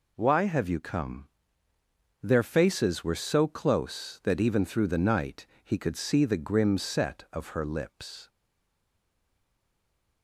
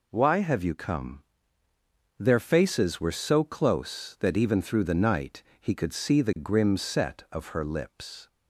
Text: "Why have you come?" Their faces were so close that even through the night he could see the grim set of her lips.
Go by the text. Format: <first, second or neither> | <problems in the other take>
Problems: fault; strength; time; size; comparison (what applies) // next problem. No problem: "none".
second | pauses between "night" and "he"; slight; at 5.4 s; 0.18 s long; slight in the second // stays silent after the last word; noticeable; from 8.2 s on; 2.0 s long